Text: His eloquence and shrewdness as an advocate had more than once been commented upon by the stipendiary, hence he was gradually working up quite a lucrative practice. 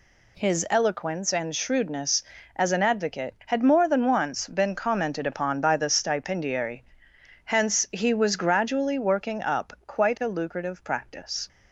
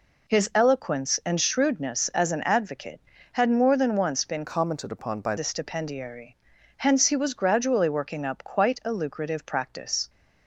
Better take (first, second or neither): first